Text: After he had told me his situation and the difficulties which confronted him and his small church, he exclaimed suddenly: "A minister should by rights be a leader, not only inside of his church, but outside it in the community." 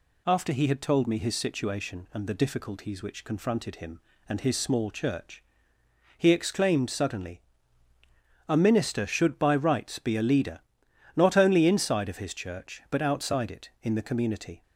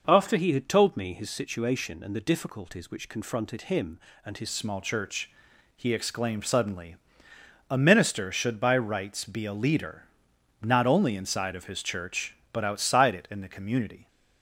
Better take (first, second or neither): first